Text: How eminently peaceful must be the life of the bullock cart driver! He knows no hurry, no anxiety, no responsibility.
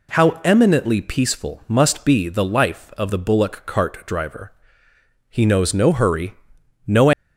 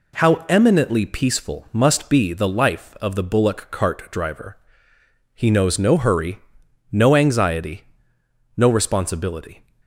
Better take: second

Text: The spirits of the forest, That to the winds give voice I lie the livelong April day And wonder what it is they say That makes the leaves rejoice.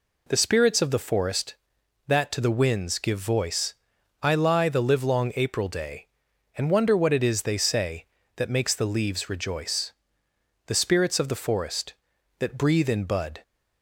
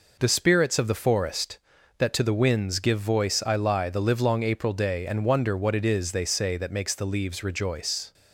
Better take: second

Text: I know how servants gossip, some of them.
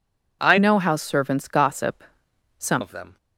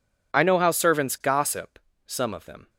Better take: second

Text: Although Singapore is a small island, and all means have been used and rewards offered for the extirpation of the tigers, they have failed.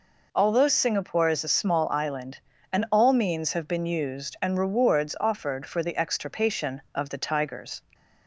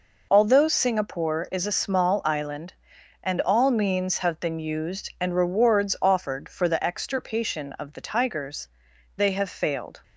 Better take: second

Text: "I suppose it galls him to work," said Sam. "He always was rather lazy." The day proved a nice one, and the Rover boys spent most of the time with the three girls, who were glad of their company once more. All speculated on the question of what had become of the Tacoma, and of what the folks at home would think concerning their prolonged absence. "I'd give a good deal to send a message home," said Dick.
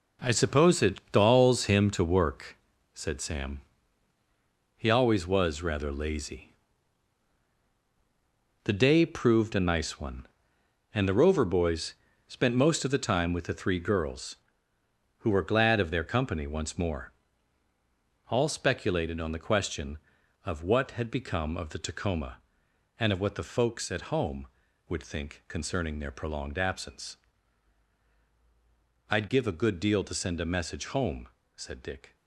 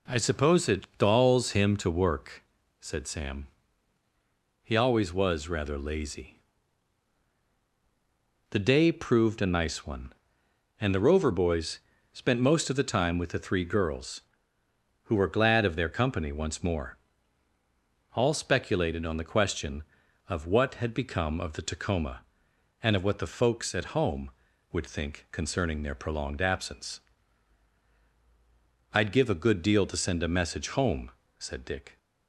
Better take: second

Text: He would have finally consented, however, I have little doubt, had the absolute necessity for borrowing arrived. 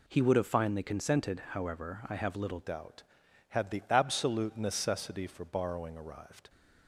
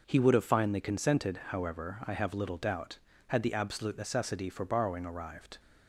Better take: second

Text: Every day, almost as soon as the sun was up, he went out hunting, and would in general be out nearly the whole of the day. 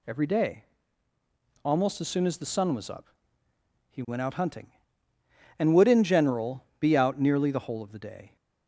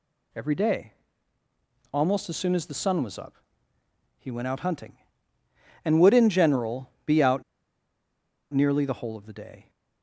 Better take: first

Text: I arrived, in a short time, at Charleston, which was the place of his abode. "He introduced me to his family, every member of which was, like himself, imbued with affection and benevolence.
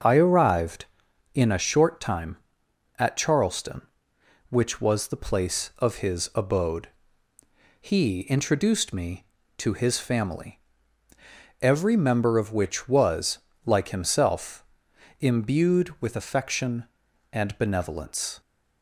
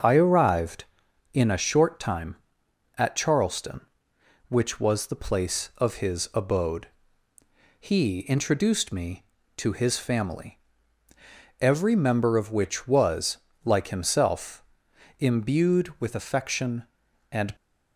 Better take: first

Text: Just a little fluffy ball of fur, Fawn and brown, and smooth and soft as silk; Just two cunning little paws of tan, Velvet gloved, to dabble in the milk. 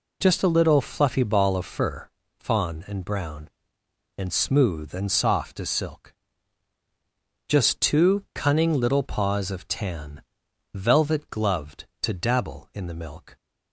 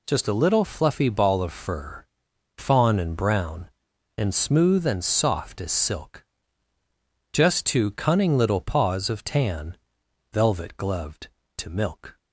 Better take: first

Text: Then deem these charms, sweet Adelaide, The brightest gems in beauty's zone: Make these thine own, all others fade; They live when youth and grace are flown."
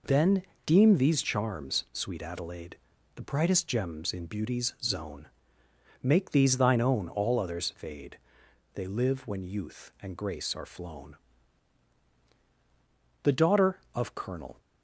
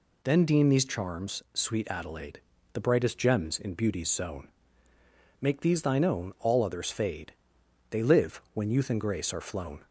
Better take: second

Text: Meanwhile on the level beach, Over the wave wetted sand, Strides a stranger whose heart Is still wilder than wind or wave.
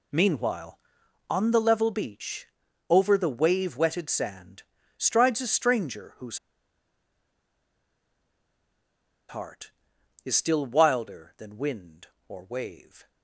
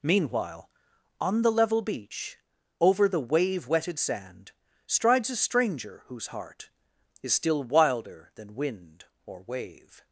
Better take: second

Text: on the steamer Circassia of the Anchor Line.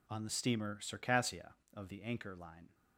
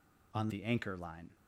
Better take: first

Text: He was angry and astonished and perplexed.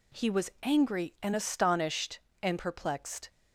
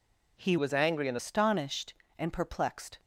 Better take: first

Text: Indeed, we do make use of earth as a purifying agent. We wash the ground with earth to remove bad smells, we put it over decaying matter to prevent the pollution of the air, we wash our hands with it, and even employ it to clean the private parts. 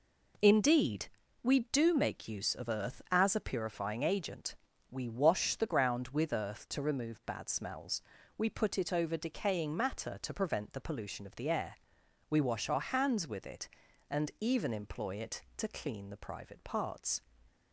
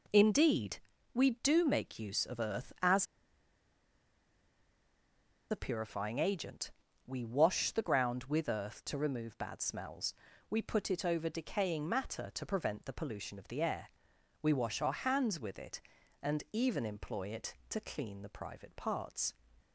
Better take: first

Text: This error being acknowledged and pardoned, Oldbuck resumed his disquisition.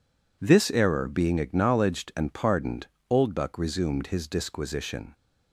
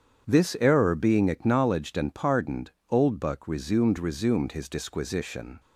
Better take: first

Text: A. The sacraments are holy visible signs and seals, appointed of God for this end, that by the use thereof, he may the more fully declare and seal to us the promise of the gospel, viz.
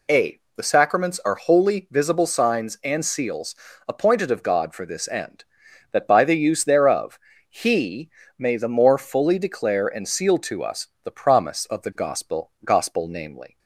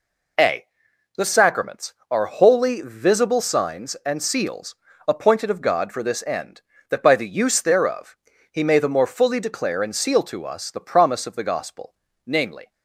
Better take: second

